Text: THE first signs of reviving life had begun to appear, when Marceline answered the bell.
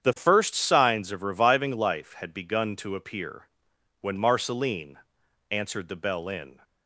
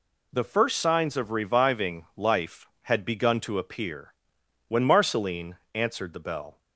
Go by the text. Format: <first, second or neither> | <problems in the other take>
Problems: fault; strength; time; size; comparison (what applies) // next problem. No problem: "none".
second | starts louder than the rest; strong; until 1.0 s; 8.5 dB // pauses between "Marceline" and "answered"; noticeable; at 4.9 s; 0.68 s long; slight in the second // goes on to say "In"; slight; from 6.2 s on; 0.32 s long